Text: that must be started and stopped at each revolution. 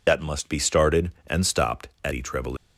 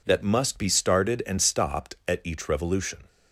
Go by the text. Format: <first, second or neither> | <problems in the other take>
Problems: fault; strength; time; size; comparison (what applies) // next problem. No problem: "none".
second | loses the start of "that"; at 0.0 s; 35 ms